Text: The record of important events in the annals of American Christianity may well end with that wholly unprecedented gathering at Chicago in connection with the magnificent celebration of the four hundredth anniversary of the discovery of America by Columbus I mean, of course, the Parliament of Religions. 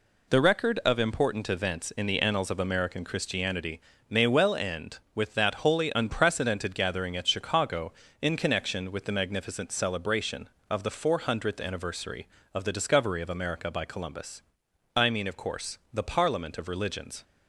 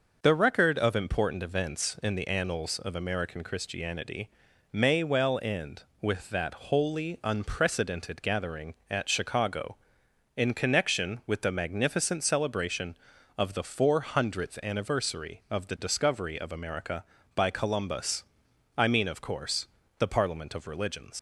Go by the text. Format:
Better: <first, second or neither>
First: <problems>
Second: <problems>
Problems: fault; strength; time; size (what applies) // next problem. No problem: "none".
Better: first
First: pauses between "Christianity" and "may"; slight; at 3.7 s; 0.30 s long // pauses between "Columbus" and "I"; noticeable; at 14.4 s; 0.56 s long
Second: pauses between "Christianity" and "may"; at 4.2 s; 0.42 s long // pauses between "that" and "wholly"; slight; at 6.5 s; 0.16 s long // pauses between "Columbus" and "I"; noticeable; at 18.2 s; 0.56 s long // leaves "Religions" unfinished; at 21.1 s; 65 ms